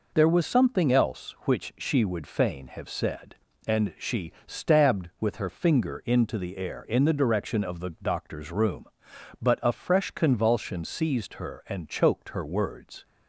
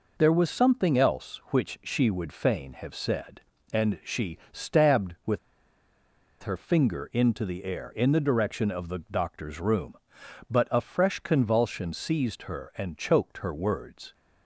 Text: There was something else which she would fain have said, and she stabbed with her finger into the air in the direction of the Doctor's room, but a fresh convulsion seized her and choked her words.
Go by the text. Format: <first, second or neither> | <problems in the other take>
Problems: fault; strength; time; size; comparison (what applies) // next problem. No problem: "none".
first | pauses between "she" and "stabbed"; slight; at 4.3 s; 0.16 s long; slight in the first // pauses between "with" and "her"; at 5.3 s; 1.0 s long